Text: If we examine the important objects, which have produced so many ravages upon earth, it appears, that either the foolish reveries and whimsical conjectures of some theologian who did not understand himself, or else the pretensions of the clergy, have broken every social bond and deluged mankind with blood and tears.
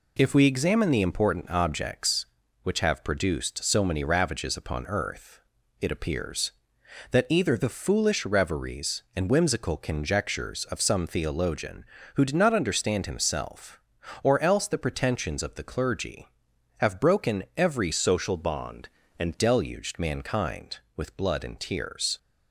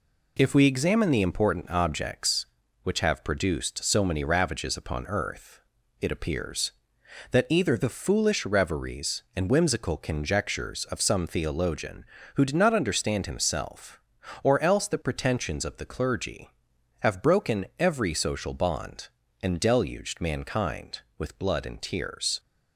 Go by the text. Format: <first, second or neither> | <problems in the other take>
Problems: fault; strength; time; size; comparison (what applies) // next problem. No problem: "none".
second | changes voice from "social" to "and"; from 17.9 to 19.3 s; 1.4 s long